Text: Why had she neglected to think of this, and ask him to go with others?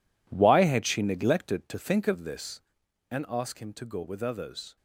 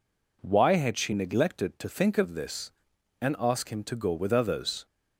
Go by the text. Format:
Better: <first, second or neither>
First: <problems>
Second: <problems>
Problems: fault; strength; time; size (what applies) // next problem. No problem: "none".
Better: second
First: gets quieter; strong; throughout; 12.5 dB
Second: none